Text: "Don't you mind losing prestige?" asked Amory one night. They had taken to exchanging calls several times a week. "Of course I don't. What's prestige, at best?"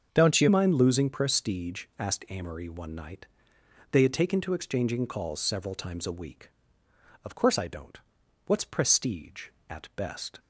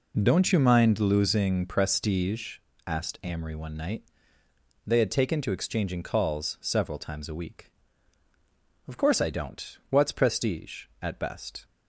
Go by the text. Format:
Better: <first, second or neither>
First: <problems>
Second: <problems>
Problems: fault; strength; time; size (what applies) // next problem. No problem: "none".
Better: second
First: starts louder than the rest; until 1.1 s; 6.5 dB // changes voice at "mind"; from 0.4 s on; 9.9 s long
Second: none